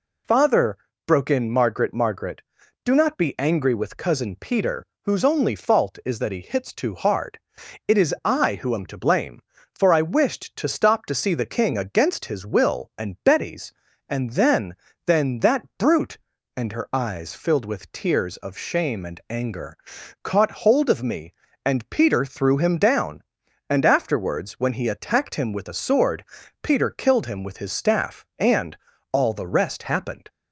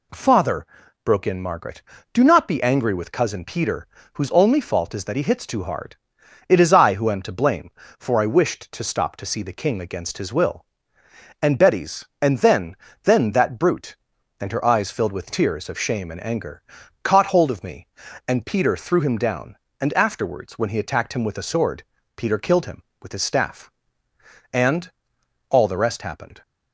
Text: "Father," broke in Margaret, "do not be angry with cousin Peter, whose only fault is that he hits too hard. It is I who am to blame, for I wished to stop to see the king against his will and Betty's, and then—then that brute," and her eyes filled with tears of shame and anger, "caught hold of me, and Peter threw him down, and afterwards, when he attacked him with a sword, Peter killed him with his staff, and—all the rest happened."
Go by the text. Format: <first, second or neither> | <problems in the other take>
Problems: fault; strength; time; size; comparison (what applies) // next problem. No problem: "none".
second | says "Margaret" twice; at 1.9 s